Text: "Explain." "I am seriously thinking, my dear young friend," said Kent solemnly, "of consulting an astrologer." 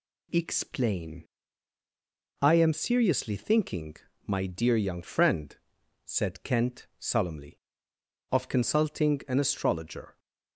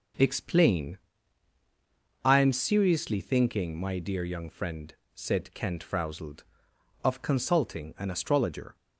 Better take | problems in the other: first | starts louder than the rest; until 2.4 s; 7 dB // says "frowsled" for "solemnly"; at 5.8 s

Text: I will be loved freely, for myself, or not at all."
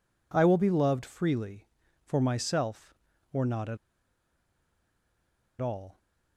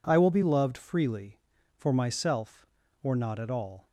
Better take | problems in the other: second | pauses between "at" and "all"; strong; at 3.7 s; 1.8 s long

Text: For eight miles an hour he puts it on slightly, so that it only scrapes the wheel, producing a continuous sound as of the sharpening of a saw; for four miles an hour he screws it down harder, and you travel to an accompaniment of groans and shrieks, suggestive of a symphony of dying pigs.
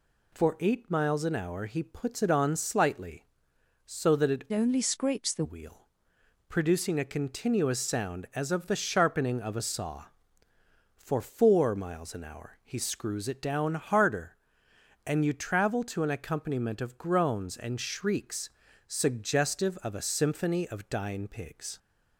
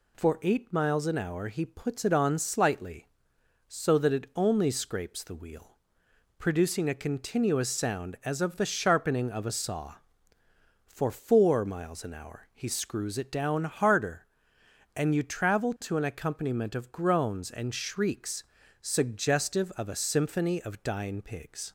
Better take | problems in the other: second | changes voice from "only" to "the"; from 4.5 to 5.4 s; 0.9 s long

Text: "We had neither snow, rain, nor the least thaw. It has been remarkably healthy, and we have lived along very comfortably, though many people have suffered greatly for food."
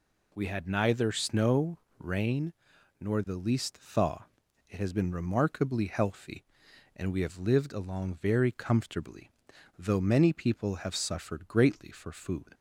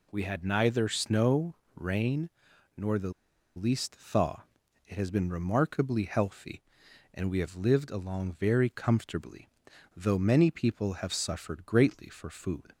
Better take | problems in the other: first | pauses between "the" and "least"; at 3.1 s; 0.45 s long

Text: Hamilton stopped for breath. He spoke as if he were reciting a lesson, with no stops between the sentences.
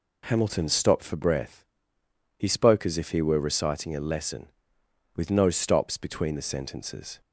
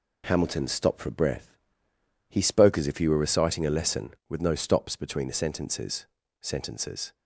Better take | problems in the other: first | says "sentences" twice; at 6.4 s

